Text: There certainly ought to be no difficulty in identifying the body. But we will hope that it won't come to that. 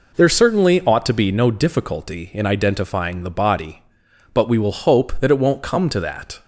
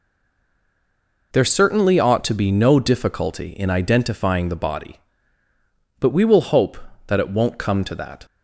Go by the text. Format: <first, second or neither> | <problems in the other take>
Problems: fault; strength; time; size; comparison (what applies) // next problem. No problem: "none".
first | stays silent before the first word; noticeable; until 1.3 s; 1.3 s long